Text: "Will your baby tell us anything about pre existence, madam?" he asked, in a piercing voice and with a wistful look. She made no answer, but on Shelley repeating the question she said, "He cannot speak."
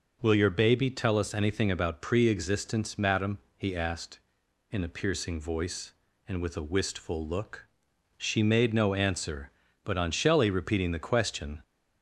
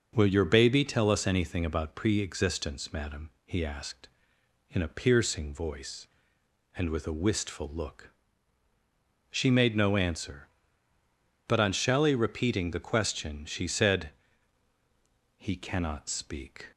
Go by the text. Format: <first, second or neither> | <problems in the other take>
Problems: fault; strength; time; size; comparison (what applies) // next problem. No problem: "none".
second | stops before "she said He cannot speak"; at 11.6 s